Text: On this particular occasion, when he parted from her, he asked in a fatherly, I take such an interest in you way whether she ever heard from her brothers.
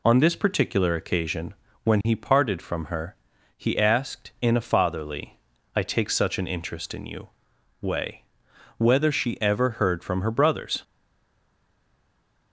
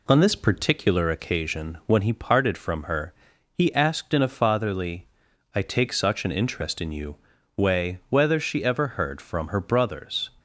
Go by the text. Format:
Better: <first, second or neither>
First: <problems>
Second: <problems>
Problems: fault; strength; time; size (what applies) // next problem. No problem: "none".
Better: second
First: pauses between "you" and "way"; noticeable; at 7.3 s; 0.52 s long // pauses between "way" and "whether"; noticeable; at 8.2 s; 0.56 s long // stays silent after the last word; noticeable; from 10.8 s on; 1.7 s long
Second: pauses between "you" and "way"; at 7.1 s; 0.40 s long